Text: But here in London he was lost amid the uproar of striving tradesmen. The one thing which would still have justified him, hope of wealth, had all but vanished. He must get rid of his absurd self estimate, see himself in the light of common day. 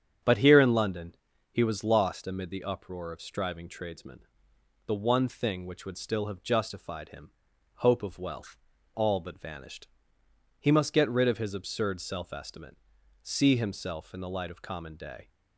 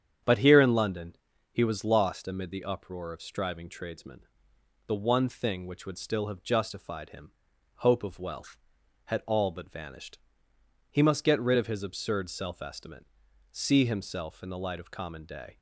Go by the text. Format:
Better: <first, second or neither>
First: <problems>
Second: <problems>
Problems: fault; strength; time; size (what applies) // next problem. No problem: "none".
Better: second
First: starts louder than the rest; strong; until 1.6 s; 8 dB // pauses between "London" and "he"; slight; at 1.1 s; 0.36 s long // skips "had"; at 8.7 s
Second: starts louder than the rest; strong; until 1.6 s; 8.5 dB // pauses between "London" and "he"; slight; at 1.1 s; 0.36 s long